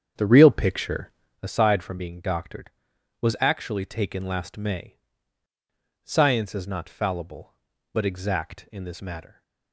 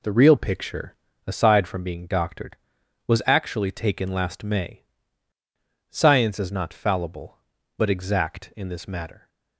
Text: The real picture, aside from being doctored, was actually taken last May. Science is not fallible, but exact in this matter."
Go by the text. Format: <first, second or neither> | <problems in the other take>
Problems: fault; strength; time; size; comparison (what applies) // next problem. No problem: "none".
second | starts louder than the rest; strong; until 1.4 s; 8 dB